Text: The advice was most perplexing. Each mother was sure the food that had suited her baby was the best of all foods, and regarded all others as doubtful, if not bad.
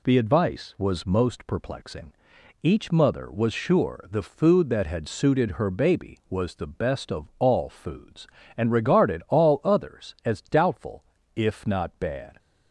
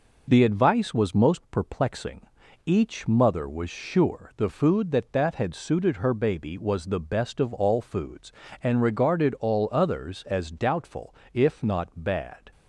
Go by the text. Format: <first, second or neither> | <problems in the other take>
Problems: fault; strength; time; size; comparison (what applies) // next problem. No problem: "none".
first | says "that" twice; at 5.1 s